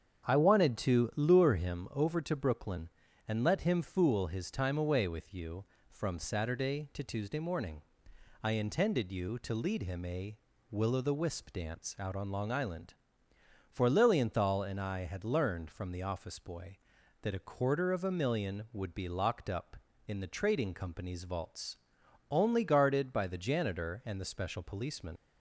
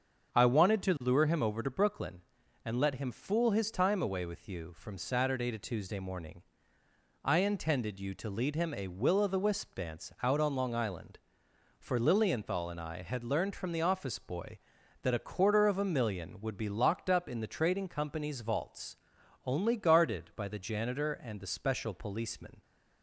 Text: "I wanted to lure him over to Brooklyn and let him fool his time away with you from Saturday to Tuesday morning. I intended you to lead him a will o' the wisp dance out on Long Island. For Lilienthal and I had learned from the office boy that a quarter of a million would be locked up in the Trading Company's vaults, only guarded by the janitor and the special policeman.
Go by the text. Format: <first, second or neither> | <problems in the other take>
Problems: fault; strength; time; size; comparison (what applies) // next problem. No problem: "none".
second | starts louder than the rest; strong; until 1.3 s; 8 dB; also in the second // leaves "policeman" unfinished; at 25.1 s; 90 ms